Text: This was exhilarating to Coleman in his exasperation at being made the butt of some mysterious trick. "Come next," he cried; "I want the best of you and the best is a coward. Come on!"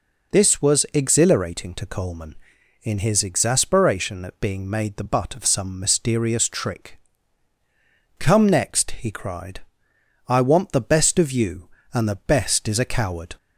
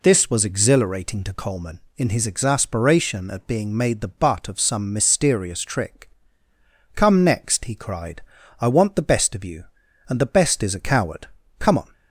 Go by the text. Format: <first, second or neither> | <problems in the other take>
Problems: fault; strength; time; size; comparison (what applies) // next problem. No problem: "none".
second | stops before "Come on"; at 13.3 s